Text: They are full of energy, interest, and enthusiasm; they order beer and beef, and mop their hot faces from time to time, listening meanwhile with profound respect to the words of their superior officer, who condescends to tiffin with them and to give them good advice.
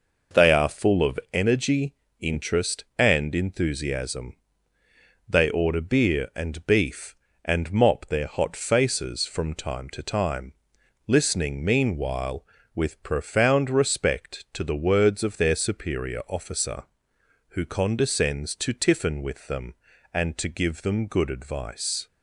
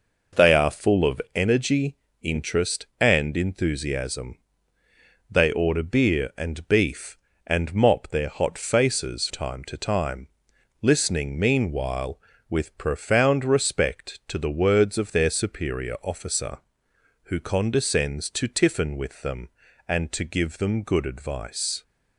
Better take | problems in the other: first | skips "from"; at 9.2 s

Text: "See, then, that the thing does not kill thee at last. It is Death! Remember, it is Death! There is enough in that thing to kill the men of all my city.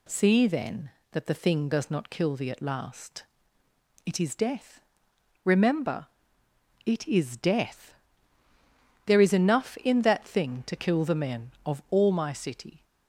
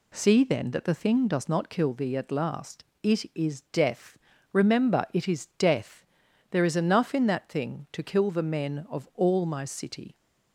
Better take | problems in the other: neither | none

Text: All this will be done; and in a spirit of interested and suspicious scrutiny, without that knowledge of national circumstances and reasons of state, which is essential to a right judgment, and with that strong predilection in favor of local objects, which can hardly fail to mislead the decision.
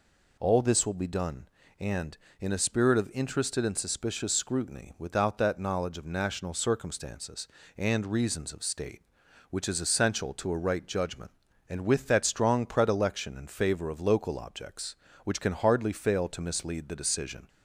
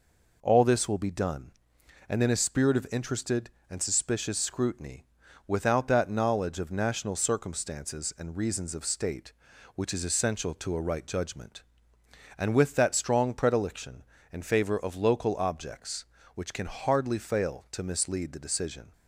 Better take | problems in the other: neither | none

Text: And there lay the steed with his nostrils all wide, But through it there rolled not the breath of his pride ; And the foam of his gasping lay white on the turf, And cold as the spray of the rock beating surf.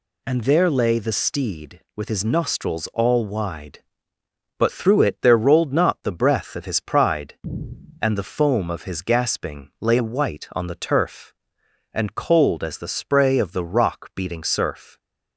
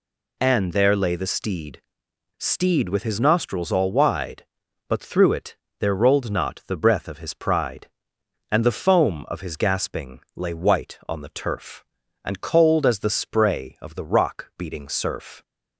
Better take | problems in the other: first | says "steed" twice; at 2.3 s // pauses between "it" and "there"; slight; at 5.5 s; 0.24 s long

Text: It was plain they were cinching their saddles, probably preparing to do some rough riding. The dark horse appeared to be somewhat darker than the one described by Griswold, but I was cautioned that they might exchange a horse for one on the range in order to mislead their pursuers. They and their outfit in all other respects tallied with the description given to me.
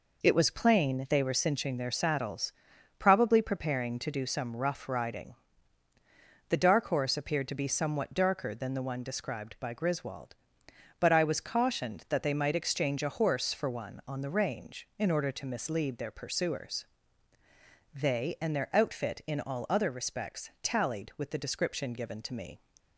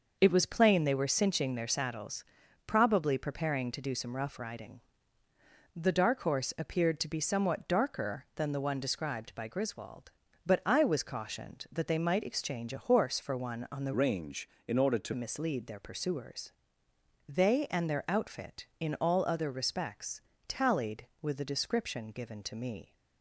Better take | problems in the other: first | changes voice from "range" to "to"; from 13.9 to 15.1 s; 1.2 s long // pauses between "respects" and "tallied"; slight; at 20.2 s; 0.26 s long

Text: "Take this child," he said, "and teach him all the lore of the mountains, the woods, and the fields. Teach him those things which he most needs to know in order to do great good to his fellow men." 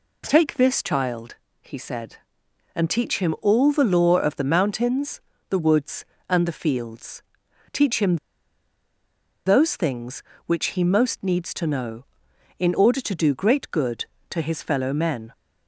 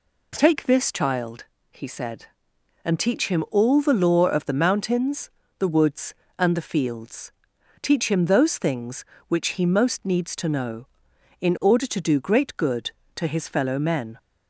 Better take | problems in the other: second | pauses between "him" and "those"; strong; at 8.1 s; 1.2 s long

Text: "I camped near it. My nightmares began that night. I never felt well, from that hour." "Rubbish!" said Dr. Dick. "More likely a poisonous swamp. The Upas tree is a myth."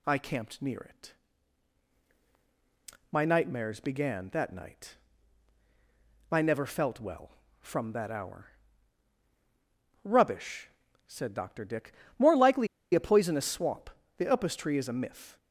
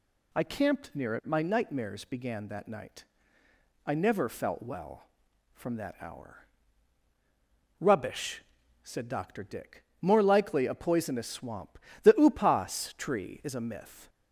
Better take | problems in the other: second | pauses between "likely" and "a"; slight; at 12.6 s; 0.27 s long

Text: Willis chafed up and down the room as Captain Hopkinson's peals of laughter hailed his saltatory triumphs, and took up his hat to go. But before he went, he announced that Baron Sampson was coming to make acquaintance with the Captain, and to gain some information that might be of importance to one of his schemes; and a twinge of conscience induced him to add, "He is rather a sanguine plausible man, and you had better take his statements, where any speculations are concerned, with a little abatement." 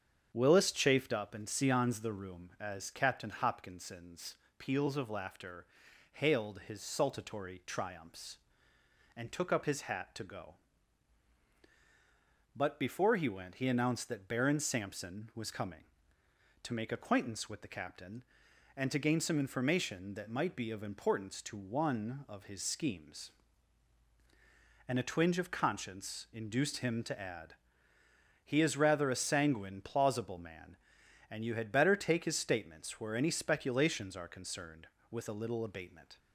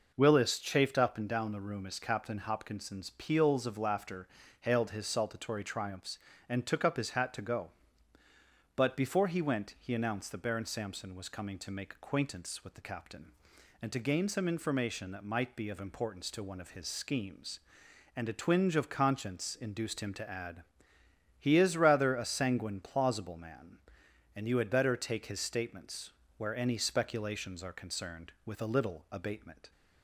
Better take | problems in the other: second | starts louder than the rest; strong; until 1.3 s; 7.5 dB // says "seons" for "down"; at 1.4 s // pauses between "Hopkinson's" and "peals"; slight; at 4.3 s; 0.22 s long // pauses between "laughter" and "hailed"; noticeable; at 5.6 s; 0.50 s long; slight in the second

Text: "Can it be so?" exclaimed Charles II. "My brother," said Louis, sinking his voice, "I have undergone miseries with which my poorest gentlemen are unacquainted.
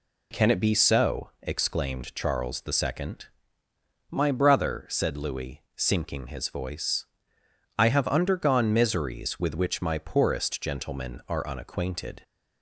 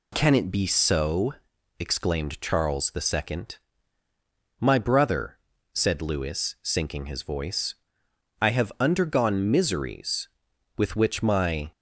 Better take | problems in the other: first | stops before "poorest gentlemen are unacquainted"; at 11.7 s

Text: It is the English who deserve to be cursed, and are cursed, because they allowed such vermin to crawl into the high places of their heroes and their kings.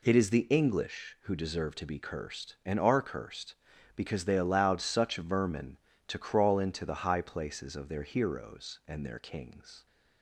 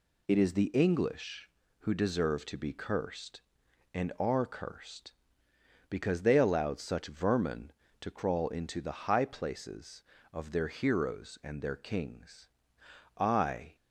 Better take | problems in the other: first | goes on to say "I"; from 13.1 s on; 0.58 s long

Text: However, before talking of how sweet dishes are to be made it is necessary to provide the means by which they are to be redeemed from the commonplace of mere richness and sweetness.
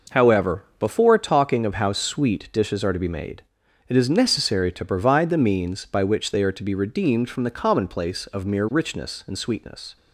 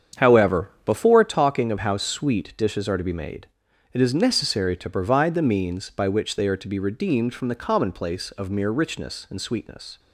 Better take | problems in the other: first | starts louder than the rest; strong; until 1.4 s; 8 dB // pauses between "made" and "it"; noticeable; at 3.4 s; 0.46 s long; noticeable in the first

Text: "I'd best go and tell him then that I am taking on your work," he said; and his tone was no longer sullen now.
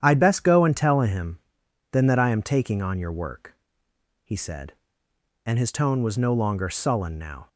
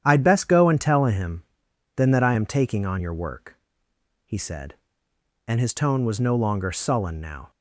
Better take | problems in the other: neither | starts louder than the rest; strong; the same in both // pauses between "him" and "then"; noticeable; the same in both

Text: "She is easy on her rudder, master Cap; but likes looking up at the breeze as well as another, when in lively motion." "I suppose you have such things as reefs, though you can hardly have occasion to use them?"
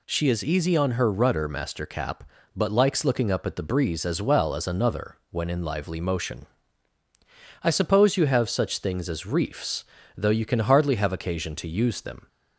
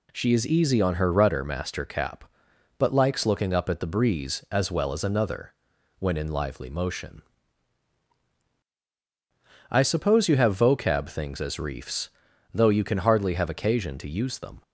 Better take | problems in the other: first | says "vocab" for "such"; at 10.5 s

